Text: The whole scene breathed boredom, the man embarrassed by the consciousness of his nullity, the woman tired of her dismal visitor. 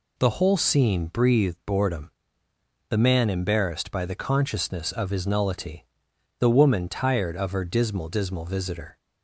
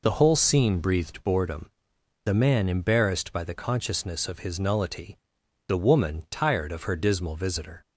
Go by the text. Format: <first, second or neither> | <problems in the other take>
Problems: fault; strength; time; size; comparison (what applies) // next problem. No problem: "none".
second | says "dismal" twice; at 8.0 s